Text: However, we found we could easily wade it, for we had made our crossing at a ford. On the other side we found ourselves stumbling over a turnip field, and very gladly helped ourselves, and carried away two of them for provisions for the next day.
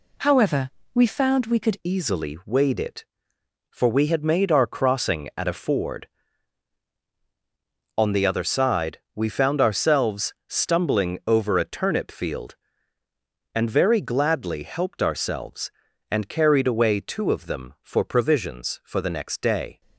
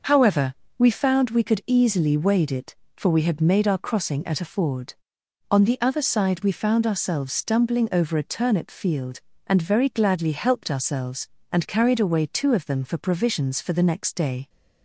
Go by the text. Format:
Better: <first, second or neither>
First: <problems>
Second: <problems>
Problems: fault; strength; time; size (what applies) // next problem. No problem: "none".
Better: second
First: changes voice at "easily"; from 1.8 s on; 18.0 s long // pauses between "side" and "we"; slight; at 8.9 s; 0.16 s long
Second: none